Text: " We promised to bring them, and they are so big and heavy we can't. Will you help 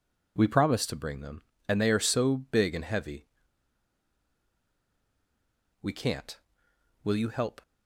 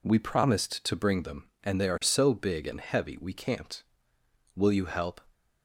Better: second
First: pauses between "heavy" and "we"; strong; at 3.2 s; 2.5 s long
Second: none

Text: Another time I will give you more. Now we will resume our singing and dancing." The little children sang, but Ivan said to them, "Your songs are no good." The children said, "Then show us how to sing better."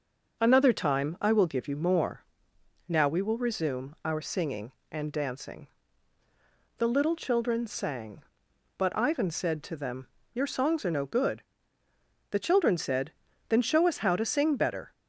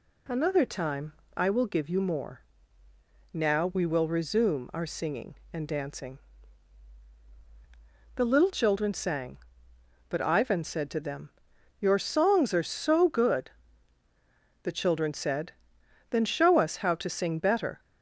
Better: first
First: none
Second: pauses between "time" and "I"; slight; at 1.1 s; 0.24 s long // says "so" for "no"; at 12.6 s

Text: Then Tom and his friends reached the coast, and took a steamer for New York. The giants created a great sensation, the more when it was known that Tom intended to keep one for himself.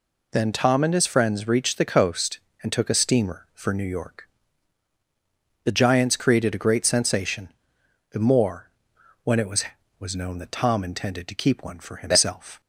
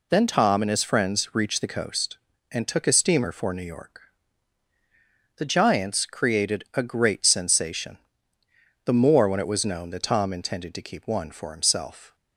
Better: second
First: pauses between "more" and "when"; noticeable; at 8.7 s; 0.52 s long // says "was" twice; at 10.0 s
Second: none

